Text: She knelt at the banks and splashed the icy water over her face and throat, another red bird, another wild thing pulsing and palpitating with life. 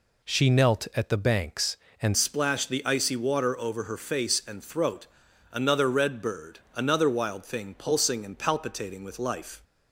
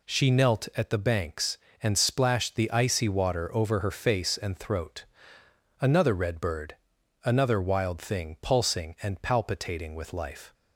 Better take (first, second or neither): second